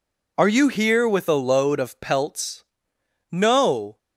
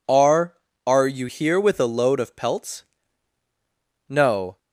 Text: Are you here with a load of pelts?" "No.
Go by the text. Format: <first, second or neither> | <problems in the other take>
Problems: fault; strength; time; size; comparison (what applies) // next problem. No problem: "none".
first | says "Are" twice; at 0.8 s